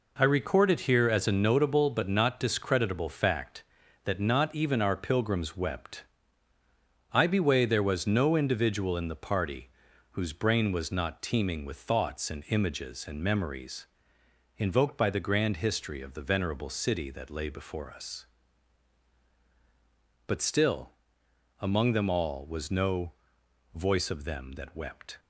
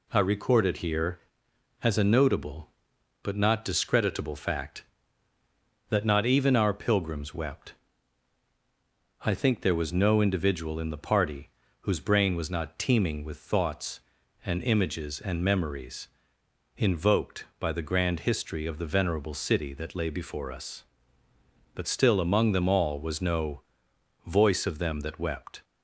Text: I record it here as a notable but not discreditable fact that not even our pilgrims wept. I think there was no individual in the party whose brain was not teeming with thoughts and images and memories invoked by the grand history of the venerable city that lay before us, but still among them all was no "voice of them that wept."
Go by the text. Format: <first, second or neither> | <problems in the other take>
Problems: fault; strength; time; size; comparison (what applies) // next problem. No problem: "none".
second | says "beway" for "think"; at 7.2 s // pauses between "party" and "whose"; at 9.6 s; 0.44 s long; slight in the second // pauses between "memories" and "invoked"; noticeable; at 13.8 s; 0.72 s long; noticeable in the second // pauses between "still" and "among"; noticeable; at 20.9 s; 0.66 s long // pauses between "no" and "voice"; noticeable; at 23.1 s; 0.64 s long; noticeable in the second